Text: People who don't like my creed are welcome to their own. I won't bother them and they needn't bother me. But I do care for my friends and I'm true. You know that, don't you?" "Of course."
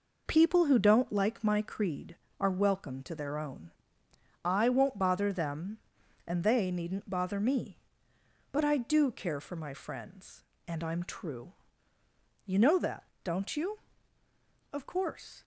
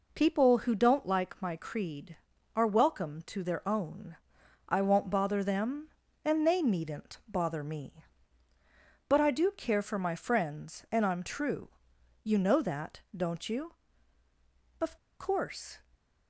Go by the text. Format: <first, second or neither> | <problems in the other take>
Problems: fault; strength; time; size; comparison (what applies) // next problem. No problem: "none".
first | pauses between "Of" and "course"; slight; at 14.9 s; 0.22 s long